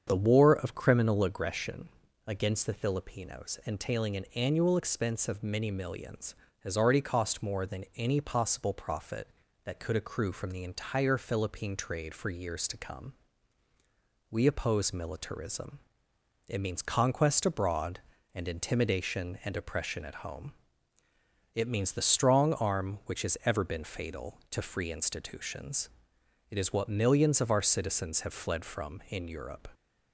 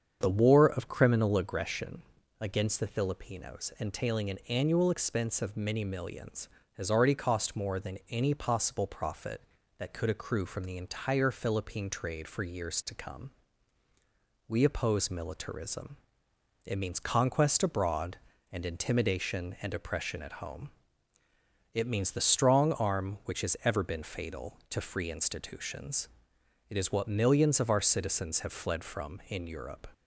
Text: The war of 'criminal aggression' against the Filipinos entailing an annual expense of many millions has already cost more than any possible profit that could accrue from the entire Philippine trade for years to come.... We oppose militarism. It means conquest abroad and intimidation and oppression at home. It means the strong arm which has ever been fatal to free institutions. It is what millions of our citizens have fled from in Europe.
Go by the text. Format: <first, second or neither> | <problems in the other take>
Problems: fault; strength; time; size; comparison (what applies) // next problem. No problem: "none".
neither | starts louder than the rest; strong; the same in both // pauses between "aggression" and "against"; slight; the same in both